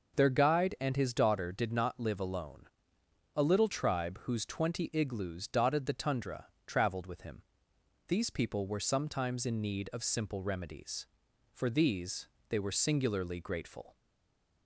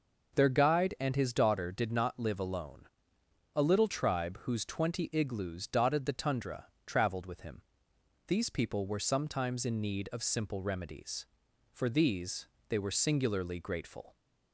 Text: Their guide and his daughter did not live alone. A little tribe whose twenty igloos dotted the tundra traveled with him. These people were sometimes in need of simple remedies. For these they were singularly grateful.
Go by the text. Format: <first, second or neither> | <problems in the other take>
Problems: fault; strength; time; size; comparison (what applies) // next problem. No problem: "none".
second | pauses between "tundra" and "traveled"; slight; at 6.4 s; 0.20 s long; slight in the second // pauses between "these" and "they"; slight; at 12.2 s; 0.20 s long; slight in the second // stays silent after the last word; slight; from 13.9 s on; 0.7 s long